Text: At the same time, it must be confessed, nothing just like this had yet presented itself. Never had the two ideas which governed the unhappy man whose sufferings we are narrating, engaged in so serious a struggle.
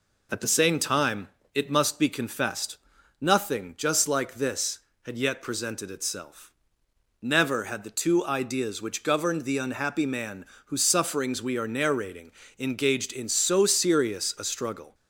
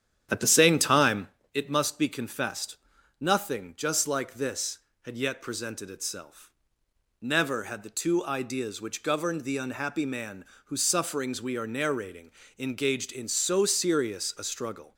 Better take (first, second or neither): first